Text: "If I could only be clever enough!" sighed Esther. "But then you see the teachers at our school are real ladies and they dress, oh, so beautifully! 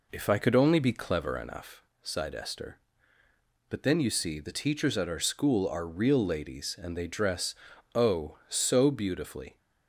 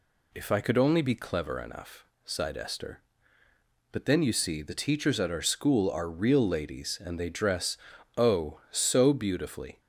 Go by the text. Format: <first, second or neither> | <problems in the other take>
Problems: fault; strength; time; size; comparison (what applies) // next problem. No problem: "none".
second | starts louder than the rest; until 1.8 s; 3.5 dB